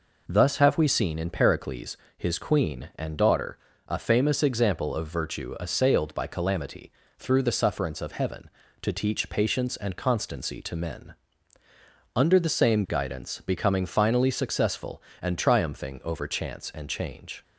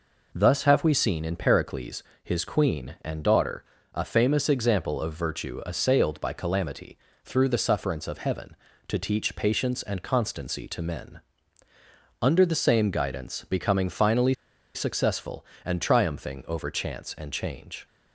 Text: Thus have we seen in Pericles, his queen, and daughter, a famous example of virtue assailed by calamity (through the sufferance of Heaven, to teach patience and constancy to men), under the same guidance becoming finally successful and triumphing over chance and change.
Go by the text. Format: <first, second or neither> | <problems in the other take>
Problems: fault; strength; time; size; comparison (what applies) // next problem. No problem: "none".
first | pauses between "finally" and "successful"; at 14.3 s; 0.42 s long